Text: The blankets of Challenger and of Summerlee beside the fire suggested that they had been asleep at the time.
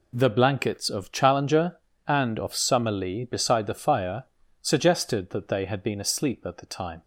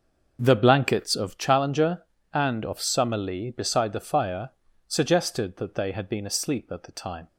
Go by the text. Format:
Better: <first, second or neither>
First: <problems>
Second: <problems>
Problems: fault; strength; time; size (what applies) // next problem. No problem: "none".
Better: first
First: pauses between "fire" and "suggested"; at 4.2 s; 0.40 s long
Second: starts louder than the rest; noticeable; until 1.4 s; 6 dB // pauses between "fire" and "suggested"; at 4.4 s; 0.40 s long